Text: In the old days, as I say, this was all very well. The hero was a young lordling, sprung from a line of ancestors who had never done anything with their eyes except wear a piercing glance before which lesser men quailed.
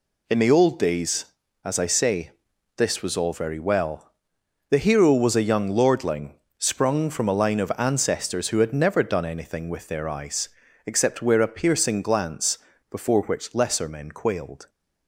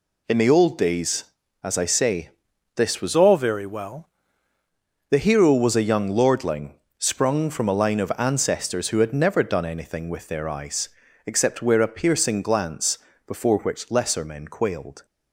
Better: first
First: pauses between "eyes" and "except"; at 10.4 s; 0.38 s long // pauses between "glance" and "before"; slight; at 12.5 s; 0.33 s long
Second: changes voice from "all" to "well"; from 3.1 to 4.0 s; 0.9 s long // pauses between "eyes" and "except"; at 10.8 s; 0.38 s long // pauses between "glance" and "before"; slight; at 12.9 s; 0.30 s long

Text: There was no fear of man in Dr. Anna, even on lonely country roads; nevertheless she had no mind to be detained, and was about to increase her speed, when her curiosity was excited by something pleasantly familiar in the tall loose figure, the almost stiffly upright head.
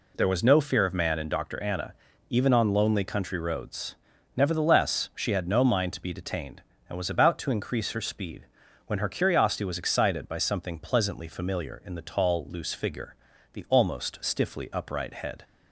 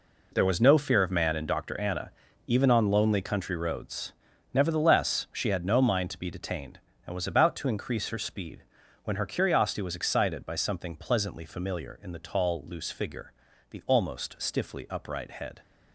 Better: first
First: none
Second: gets quieter; strong; throughout; 11.5 dB

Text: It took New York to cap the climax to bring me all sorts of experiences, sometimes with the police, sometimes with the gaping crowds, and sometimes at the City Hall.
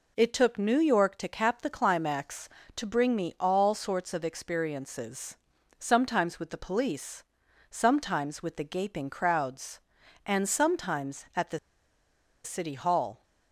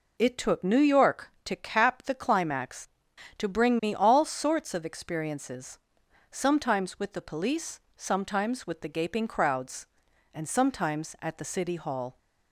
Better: second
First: pauses between "the" and "City"; noticeable; at 11.5 s; 0.86 s long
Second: none

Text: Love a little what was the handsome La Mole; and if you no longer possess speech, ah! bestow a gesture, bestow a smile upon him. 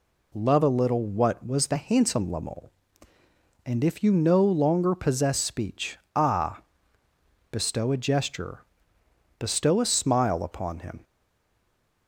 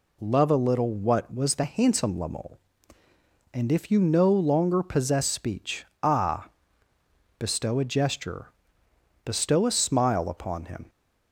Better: second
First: stays silent after the last word; from 11.0 s on; 1.0 s long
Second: none

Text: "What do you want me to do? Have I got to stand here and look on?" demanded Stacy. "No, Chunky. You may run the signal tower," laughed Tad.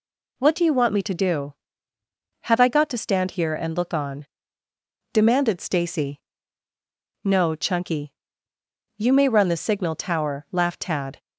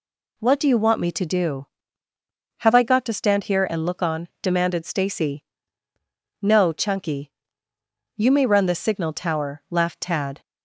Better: neither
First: none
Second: none

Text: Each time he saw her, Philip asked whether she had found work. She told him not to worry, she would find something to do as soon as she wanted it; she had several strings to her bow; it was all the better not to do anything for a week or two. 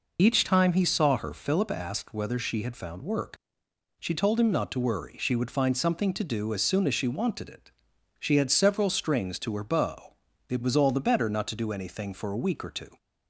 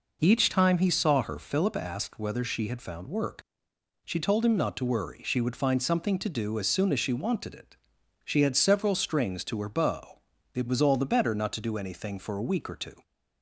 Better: second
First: loses the start of "Each"; at 0.1 s; 40 ms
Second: none

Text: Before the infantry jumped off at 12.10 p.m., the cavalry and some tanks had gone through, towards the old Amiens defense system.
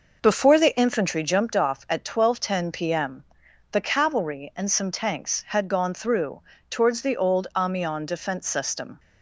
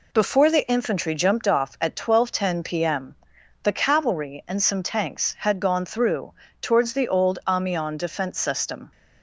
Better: second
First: starts louder than the rest; noticeable; until 1.3 s; 5.5 dB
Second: none

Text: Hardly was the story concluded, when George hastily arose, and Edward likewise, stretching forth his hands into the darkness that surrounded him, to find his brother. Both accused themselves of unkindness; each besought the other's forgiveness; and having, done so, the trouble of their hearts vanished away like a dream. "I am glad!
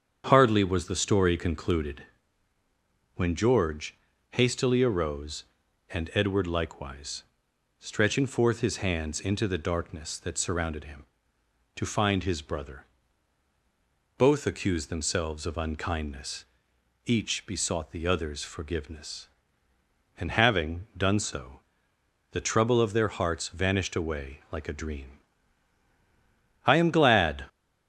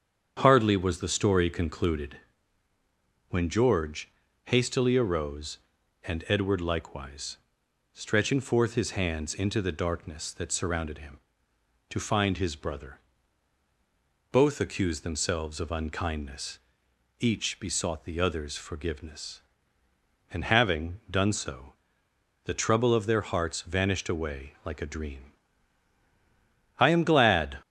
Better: neither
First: starts louder than the rest; strong; until 1.2 s; 7.5 dB // pauses between "George" and "hastily"; slight; at 3.9 s; 0.32 s long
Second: starts louder than the rest; strong; until 1.4 s; 7.5 dB // pauses between "George" and "hastily"; slight; at 4.1 s; 0.32 s long

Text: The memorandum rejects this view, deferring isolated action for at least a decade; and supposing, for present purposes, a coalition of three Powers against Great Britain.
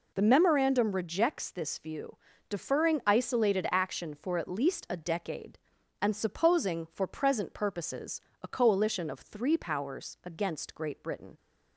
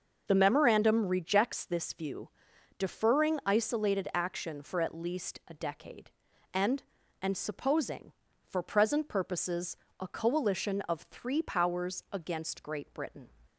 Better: first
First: none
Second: says "and" twice; at 7.2 s

